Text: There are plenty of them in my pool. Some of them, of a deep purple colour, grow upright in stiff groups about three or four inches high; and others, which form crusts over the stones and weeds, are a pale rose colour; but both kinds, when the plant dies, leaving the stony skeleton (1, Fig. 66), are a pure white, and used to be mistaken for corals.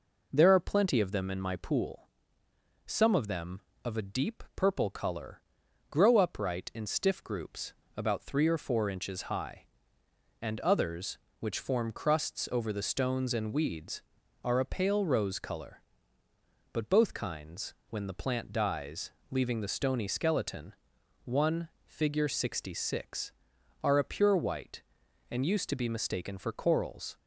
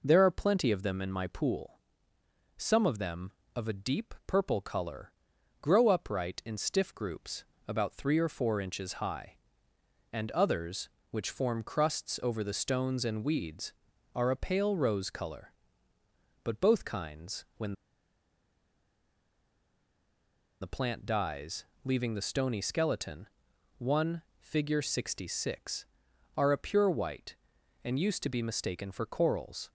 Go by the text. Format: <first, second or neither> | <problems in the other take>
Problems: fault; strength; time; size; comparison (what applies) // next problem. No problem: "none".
first | pauses between "groups" and "about"; slight; at 7.4 s; 0.24 s long; slight in the first // pauses between "when" and "the"; strong; at 17.7 s; 2.8 s long